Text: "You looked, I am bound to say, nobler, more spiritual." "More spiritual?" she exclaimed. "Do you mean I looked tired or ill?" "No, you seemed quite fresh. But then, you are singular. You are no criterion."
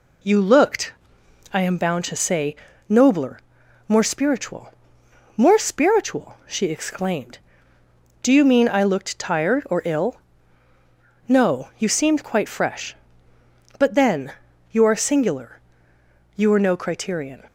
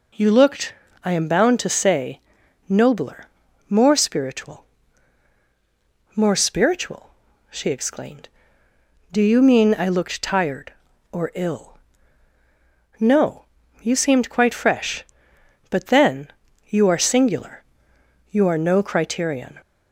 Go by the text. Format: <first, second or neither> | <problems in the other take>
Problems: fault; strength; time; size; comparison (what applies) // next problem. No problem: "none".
neither | none